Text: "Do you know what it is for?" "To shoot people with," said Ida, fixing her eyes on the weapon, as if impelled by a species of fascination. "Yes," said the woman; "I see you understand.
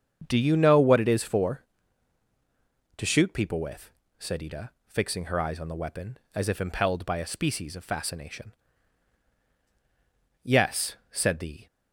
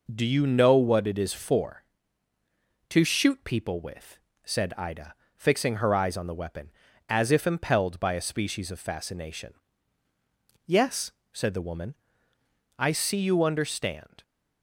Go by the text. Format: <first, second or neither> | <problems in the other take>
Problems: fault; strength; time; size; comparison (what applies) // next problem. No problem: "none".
second | starts louder than the rest; strong; until 1.2 s; 7.5 dB // stops before "woman I see you understand"; at 11.6 s